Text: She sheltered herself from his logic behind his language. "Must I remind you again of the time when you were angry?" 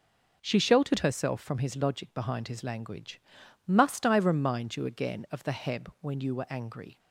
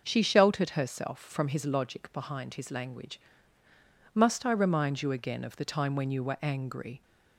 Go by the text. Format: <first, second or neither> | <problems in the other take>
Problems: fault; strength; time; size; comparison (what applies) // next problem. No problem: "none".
second | says "heb" for "time"; at 5.5 s